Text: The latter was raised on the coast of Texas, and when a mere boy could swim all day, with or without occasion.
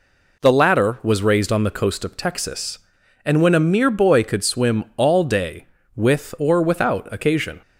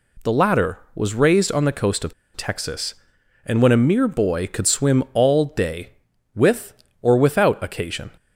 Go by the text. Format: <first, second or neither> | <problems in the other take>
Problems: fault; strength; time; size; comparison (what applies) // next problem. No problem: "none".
first | pauses between "of" and "Texas"; slight; at 2.1 s; 0.23 s long